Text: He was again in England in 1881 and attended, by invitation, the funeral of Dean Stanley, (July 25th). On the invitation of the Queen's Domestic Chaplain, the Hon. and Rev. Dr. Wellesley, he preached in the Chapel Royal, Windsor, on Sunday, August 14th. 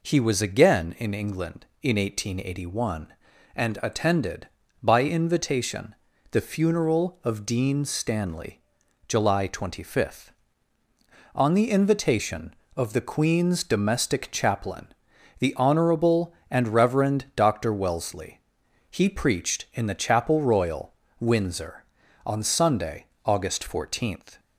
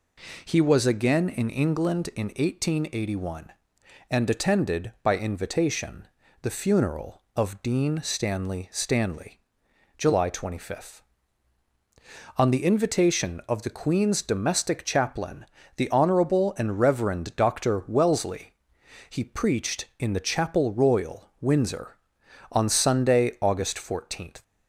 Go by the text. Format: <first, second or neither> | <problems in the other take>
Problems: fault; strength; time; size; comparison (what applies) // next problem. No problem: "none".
first | says "Stanley" twice; at 8.7 s